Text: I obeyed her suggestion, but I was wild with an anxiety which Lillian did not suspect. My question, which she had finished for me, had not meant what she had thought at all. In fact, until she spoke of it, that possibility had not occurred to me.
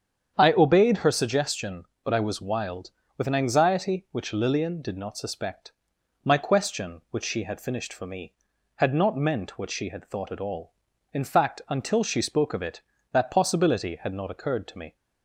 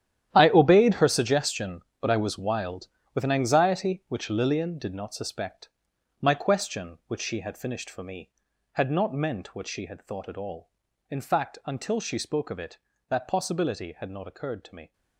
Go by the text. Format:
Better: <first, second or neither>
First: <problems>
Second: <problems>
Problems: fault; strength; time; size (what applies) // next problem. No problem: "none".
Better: first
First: starts louder than the rest; strong; until 1.3 s; 8 dB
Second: gets quieter; strong; throughout; 14 dB // starts louder than the rest; strong; until 1.3 s; 11 dB